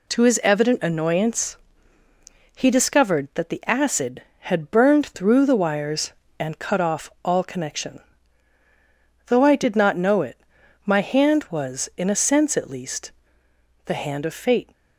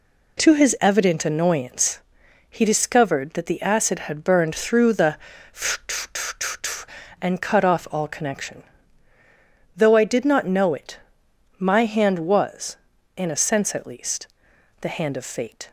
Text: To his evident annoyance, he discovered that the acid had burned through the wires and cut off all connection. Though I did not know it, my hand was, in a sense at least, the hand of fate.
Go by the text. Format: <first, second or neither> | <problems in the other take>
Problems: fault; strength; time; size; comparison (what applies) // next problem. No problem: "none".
first | skips "wires"; at 6.1 s